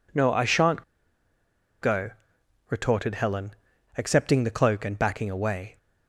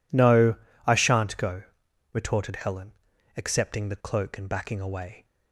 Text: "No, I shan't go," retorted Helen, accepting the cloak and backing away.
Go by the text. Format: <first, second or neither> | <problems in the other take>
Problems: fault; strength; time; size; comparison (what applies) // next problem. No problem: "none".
second | pauses between "shan't" and "go"; at 0.8 s; 1.0 s long